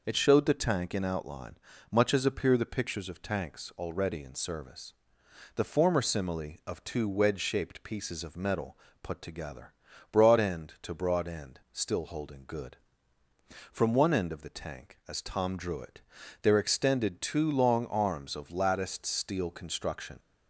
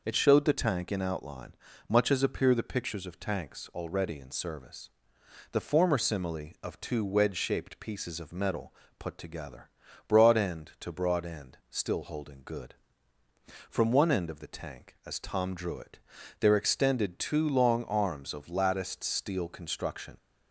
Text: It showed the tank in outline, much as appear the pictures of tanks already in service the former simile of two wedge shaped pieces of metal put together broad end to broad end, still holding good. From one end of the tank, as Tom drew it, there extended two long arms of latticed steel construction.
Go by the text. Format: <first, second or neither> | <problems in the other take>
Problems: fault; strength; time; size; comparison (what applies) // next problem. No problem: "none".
neither | pauses between "service" and "the"; noticeable; the same in both // pauses between "metal" and "put"; slight; the same in both // pauses between "together" and "broad"; the same in both